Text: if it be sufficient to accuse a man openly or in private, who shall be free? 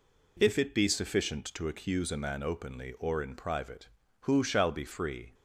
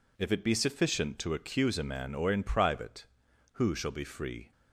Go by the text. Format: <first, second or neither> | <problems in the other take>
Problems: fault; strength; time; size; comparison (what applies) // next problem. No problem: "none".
first | skips "openly"; at 2.1 s